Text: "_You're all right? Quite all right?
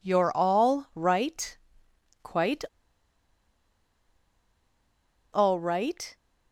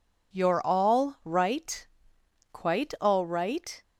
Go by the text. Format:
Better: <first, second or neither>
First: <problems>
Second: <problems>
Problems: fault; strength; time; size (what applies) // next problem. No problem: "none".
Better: second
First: pauses between "Quite" and "all"; strong; at 2.6 s; 2.7 s long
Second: none